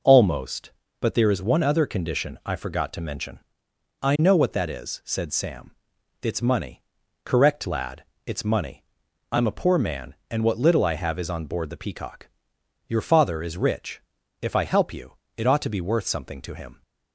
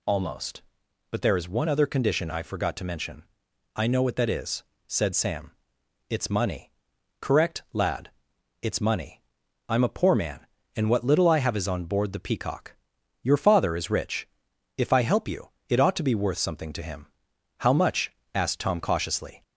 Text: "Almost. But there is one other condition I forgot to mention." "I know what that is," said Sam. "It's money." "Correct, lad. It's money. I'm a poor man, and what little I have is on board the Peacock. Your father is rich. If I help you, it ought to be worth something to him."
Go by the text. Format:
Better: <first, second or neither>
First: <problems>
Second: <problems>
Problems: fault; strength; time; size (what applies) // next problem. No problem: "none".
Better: first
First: none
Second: goes on to say "How much asked Tom cautiously"; strong; from 17.5 s on; 1.8 s long